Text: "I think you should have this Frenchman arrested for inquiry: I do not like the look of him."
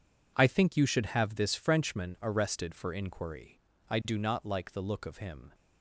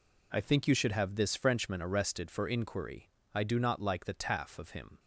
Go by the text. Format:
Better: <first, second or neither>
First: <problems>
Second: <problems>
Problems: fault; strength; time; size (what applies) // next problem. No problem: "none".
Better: first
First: none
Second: says "taff" for "look"; at 4.1 s